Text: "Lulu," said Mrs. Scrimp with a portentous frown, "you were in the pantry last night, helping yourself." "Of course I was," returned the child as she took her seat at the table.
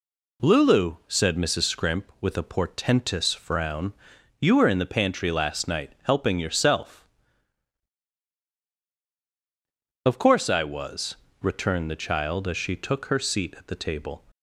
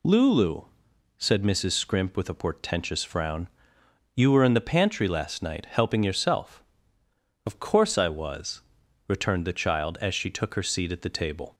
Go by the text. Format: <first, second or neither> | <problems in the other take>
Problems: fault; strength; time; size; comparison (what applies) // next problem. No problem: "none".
neither | none